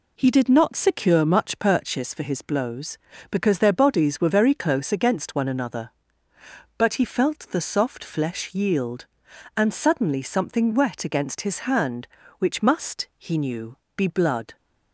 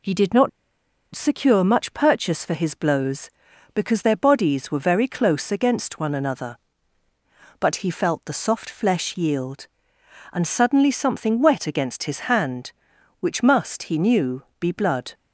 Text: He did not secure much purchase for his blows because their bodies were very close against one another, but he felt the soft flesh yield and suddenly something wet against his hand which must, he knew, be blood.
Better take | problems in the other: first | pauses between "not" and "secure"; noticeable; at 0.4 s; 0.63 s long

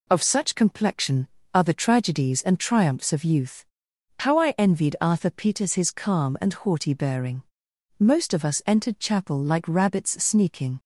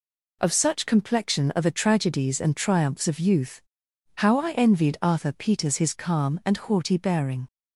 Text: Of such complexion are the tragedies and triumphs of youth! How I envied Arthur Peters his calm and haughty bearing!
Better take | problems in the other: second | goes on to say "Most of us entered chapel like rabbits sneaking"; strong; from 7.9 s on; 2.8 s long

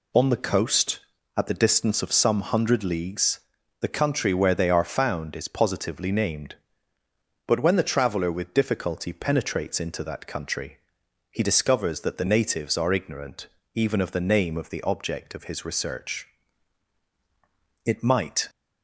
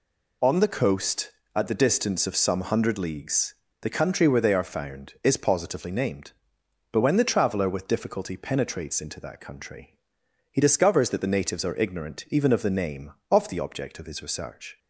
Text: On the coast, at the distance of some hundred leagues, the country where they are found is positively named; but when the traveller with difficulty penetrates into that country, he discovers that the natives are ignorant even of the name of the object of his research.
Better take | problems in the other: second | pauses between "ignorant" and "even"; slight; at 13.4 s; 0.26 s long // goes on to say "It might"; noticeable; from 17.8 s on; 0.64 s long

